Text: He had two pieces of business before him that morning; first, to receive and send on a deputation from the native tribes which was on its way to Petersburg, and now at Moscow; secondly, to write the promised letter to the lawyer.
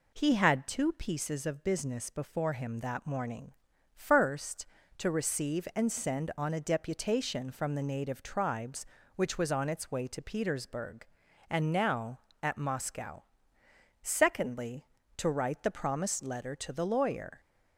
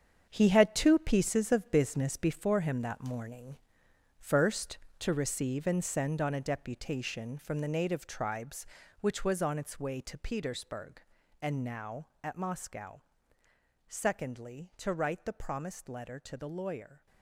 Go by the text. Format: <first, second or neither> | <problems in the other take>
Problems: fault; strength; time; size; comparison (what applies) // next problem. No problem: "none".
first | gets quieter; strong; throughout; 10.5 dB